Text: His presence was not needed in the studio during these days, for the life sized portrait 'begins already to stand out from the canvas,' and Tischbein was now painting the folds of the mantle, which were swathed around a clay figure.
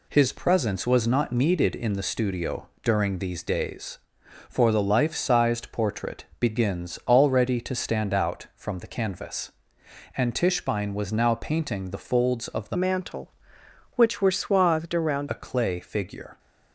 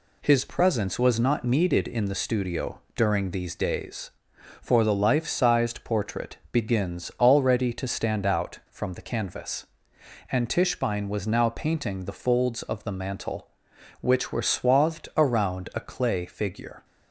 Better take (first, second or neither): second